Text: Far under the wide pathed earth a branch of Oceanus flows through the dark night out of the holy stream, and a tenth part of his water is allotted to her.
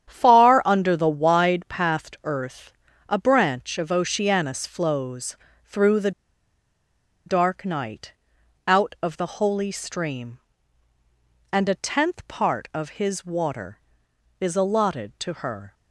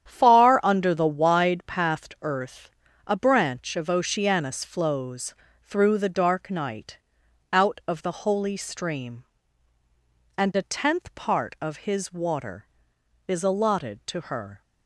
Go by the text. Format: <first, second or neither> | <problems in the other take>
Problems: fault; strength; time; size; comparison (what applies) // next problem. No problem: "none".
second | starts louder than the rest; strong; until 1.1 s; 9.5 dB; strong in the second // pauses between "earth" and "a"; at 2.7 s; 0.38 s long; also in the second // pauses between "flows" and "through"; slight; at 5.3 s; 0.30 s long; slight in the second // pauses between "the" and "dark"; at 6.1 s; 1.1 s long // pauses between "night" and "out"; noticeable; at 8.1 s; 0.56 s long; noticeable in the second